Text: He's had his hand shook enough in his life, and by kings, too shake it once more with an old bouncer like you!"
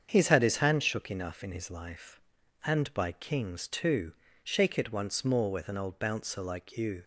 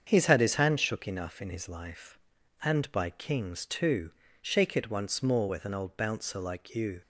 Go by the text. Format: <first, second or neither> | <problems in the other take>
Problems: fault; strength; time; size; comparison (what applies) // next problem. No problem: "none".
neither | starts louder than the rest; strong; the same in both // pauses between "too" and "shake"; slight; the same in both